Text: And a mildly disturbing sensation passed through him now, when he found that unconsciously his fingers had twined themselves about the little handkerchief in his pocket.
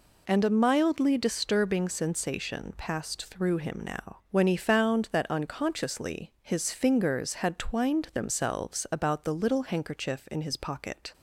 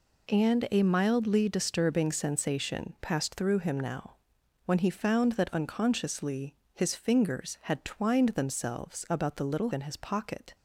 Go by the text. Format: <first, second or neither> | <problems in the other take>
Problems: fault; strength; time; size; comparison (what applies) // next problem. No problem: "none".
first | pauses between "unconsciously" and "his"; slight; at 6.5 s; 0.18 s long // skips "handkerchief"; at 9.7 s